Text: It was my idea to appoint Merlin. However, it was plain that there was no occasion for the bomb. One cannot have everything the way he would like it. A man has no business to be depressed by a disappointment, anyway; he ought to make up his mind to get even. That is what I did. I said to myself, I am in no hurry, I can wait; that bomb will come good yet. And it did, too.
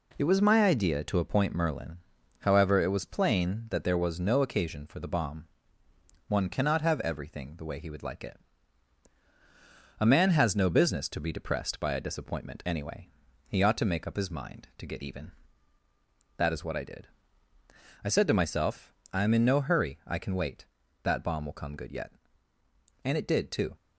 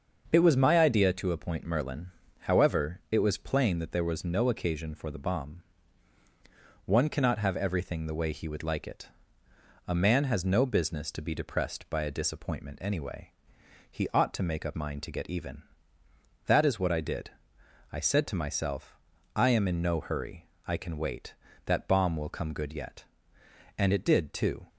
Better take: first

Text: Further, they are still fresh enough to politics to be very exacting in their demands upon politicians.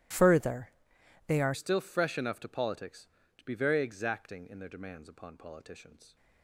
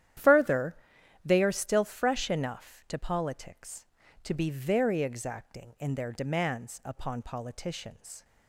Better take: second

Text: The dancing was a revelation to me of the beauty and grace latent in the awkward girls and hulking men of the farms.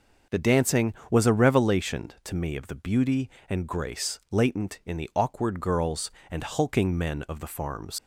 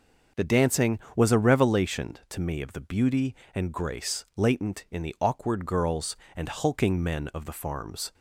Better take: second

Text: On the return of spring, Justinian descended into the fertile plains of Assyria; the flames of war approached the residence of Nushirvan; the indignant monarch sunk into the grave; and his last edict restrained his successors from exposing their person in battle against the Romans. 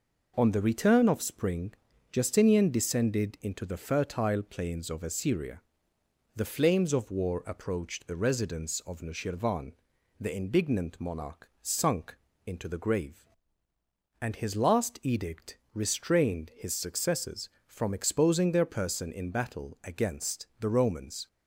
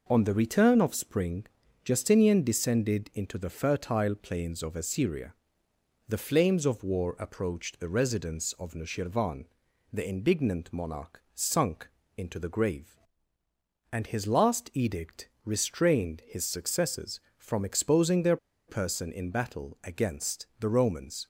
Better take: first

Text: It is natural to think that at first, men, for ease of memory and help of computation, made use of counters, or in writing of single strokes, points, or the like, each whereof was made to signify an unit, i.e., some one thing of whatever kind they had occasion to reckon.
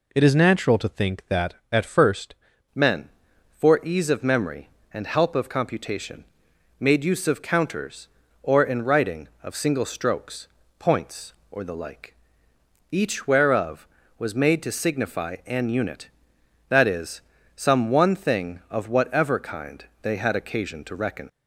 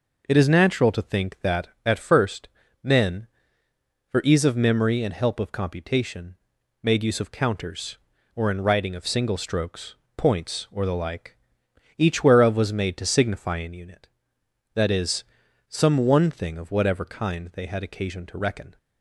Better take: second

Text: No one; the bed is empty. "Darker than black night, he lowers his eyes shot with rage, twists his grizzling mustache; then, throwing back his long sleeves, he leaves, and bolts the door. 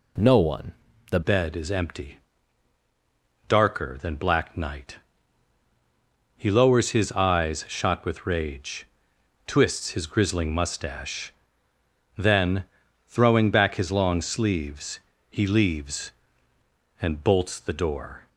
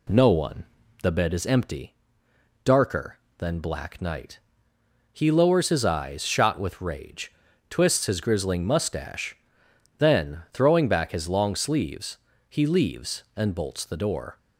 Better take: second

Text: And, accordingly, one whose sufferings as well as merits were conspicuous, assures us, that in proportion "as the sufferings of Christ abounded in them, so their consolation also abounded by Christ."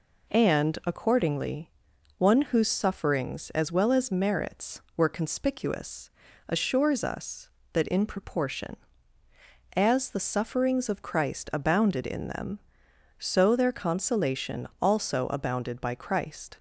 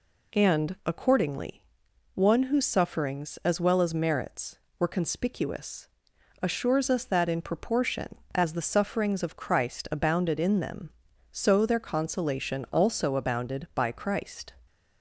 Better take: neither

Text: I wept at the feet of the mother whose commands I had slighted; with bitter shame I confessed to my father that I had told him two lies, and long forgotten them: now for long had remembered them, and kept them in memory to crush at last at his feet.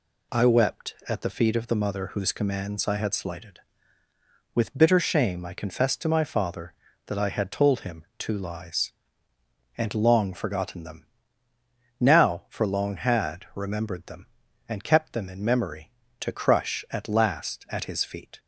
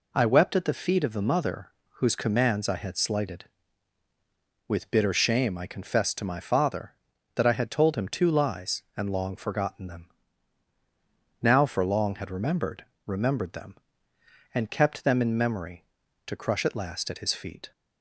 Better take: first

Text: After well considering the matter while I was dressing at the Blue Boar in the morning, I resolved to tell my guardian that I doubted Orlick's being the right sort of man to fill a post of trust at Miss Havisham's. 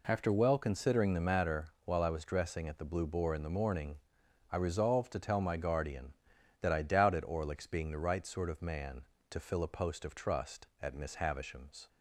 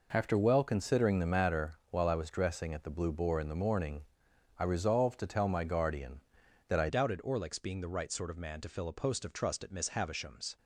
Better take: first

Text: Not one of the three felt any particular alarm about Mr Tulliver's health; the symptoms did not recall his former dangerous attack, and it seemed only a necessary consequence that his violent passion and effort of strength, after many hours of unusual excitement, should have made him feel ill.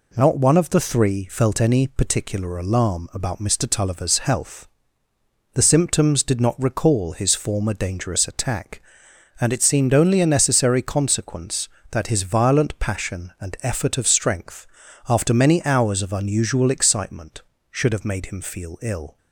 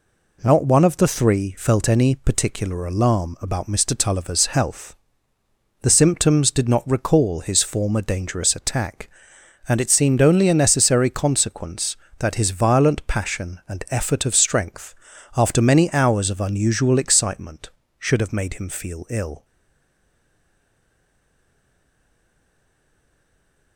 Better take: first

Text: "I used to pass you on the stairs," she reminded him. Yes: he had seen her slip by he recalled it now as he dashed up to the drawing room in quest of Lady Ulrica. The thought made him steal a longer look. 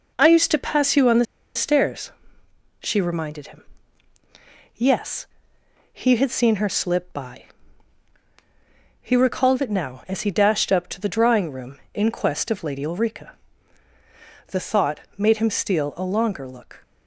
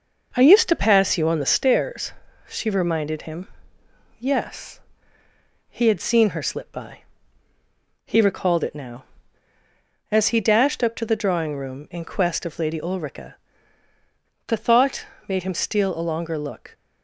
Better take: second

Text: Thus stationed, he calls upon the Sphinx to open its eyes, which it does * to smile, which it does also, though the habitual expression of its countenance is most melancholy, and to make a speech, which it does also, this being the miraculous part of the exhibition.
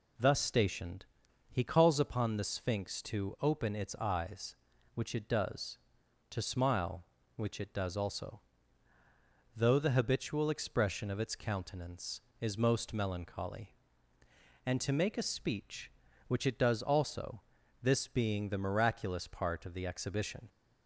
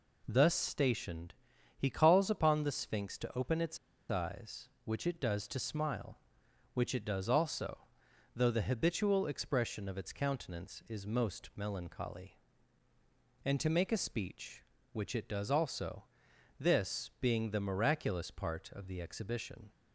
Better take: first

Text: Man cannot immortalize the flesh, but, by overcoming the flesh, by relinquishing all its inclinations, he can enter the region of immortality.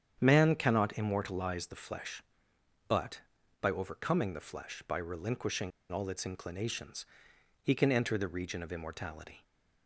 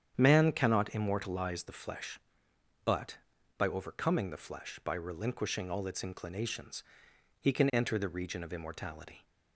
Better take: second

